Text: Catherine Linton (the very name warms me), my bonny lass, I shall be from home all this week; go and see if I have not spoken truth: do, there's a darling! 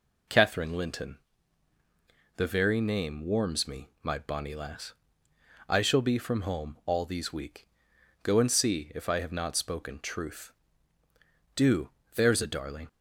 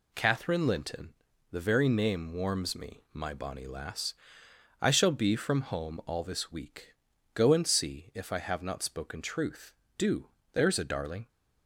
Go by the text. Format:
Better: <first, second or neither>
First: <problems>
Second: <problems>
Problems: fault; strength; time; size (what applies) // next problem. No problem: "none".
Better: second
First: says "these" for "this"; at 7.0 s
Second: none